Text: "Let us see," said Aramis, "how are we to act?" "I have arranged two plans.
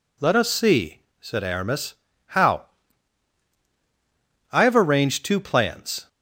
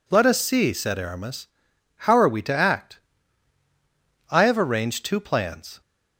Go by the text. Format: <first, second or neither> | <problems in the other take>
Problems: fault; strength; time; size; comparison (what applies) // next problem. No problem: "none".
second | skips "are we to act"; at 3.5 s